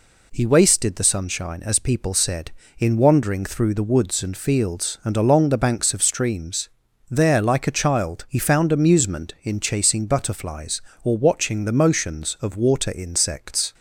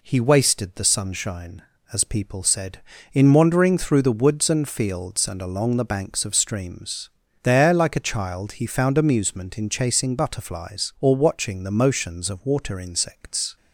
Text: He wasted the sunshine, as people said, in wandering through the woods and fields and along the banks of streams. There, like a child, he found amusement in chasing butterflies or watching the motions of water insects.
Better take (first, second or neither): neither